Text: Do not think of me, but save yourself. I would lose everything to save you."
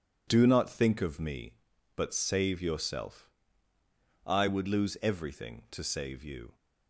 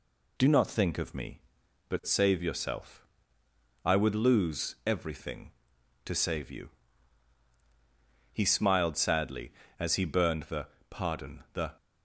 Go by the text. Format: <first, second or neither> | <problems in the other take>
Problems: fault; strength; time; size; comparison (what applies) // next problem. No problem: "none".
first | goes on to say "He smiled sadly as he burned the pardon The"; strong; from 8.3 s on; 3.4 s long